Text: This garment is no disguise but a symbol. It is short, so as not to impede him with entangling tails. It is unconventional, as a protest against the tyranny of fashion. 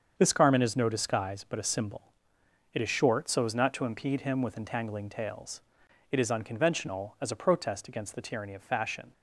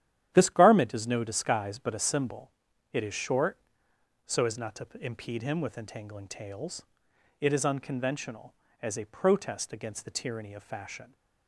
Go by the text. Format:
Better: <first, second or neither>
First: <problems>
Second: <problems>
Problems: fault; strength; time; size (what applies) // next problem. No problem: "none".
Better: first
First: starts louder than the rest; until 1.1 s; 7 dB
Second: gets quieter; strong; throughout; 9.5 dB // starts louder than the rest; strong; until 1.3 s; 11 dB